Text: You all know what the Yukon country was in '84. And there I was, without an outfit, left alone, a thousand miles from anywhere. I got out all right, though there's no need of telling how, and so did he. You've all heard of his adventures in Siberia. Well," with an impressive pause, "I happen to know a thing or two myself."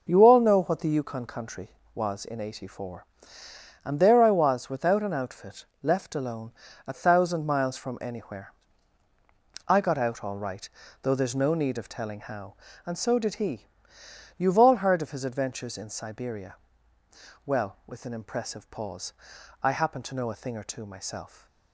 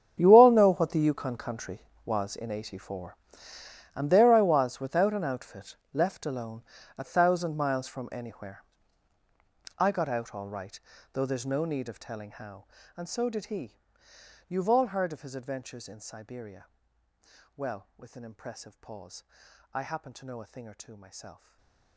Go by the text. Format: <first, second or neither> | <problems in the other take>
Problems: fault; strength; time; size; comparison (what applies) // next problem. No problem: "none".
first | gets quieter; strong; throughout; 18 dB // stays silent after the last word; slight; from 21.3 s on; 0.6 s long